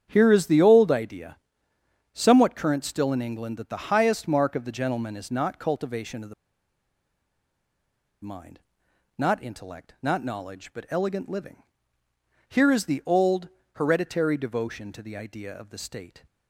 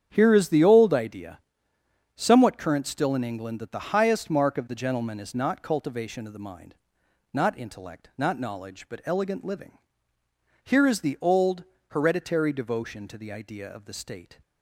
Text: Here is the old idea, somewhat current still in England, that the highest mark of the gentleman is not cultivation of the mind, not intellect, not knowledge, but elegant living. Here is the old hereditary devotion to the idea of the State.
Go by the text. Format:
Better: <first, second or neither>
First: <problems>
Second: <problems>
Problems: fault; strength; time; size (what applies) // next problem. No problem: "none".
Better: second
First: starts louder than the rest; strong; until 1.1 s; 8.5 dB // pauses between "the" and "mind"; strong; at 6.3 s; 1.9 s long // pauses between "old" and "hereditary"; slight; at 13.4 s; 0.28 s long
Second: starts louder than the rest; strong; until 1.1 s; 8.5 dB // pauses between "old" and "hereditary"; slight; at 11.6 s; 0.28 s long